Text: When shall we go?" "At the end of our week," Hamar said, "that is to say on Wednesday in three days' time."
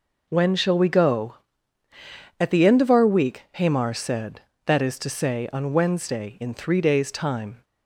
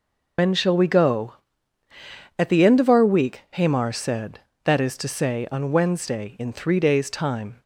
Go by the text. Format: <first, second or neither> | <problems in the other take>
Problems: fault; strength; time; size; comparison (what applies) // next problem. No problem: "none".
first | loses the start of "When"; at 0.3 s; 100 ms